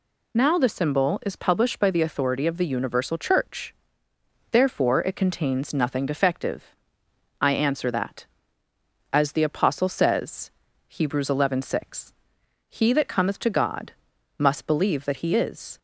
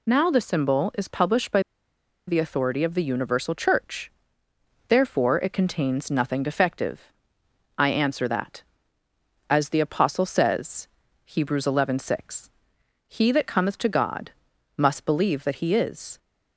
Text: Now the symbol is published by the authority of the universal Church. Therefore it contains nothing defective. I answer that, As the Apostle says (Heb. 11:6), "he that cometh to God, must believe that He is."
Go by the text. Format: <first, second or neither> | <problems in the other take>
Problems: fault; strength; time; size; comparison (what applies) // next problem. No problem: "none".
first | pauses between "by" and "the"; noticeable; at 1.6 s; 0.66 s long